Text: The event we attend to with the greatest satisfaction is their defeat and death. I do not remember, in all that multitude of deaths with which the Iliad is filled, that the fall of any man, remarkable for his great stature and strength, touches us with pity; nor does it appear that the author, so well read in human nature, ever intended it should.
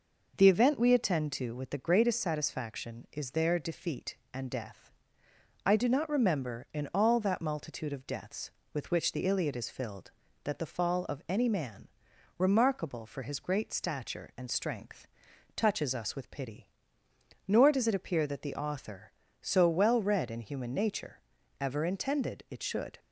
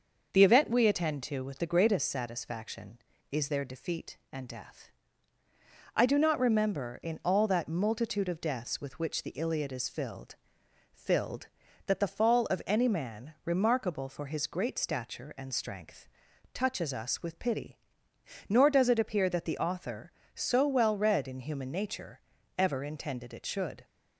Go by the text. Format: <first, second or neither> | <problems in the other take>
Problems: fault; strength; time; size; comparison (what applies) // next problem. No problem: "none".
first | starts louder than the rest; until 1.3 s; 6 dB // says "filled" twice; at 10.9 s